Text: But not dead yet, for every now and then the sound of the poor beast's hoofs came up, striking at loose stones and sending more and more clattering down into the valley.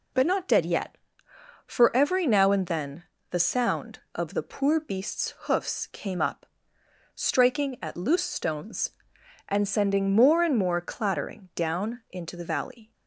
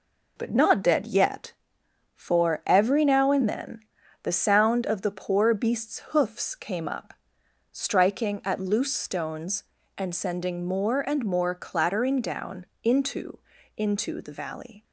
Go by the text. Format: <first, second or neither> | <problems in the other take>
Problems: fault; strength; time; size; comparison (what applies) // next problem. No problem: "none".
first | pauses between "then" and "the"; at 3.8 s; 0.42 s long; slight in the first // pauses between "down" and "into"; slight; at 12.6 s; 0.18 s long // says "into" twice; at 13.7 s